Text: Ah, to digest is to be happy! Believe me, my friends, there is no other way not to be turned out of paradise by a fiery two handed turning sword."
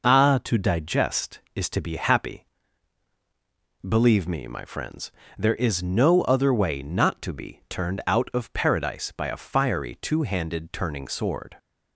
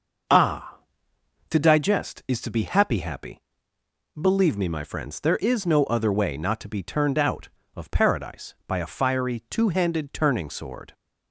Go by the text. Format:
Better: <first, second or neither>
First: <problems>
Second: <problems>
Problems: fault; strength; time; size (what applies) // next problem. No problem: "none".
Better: first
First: none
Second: says "happy" twice; at 2.9 s